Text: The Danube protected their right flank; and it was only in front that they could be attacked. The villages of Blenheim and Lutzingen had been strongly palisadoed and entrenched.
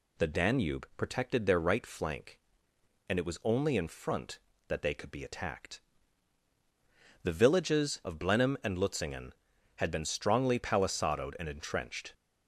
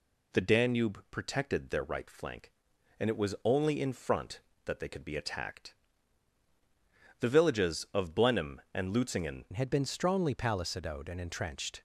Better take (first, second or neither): first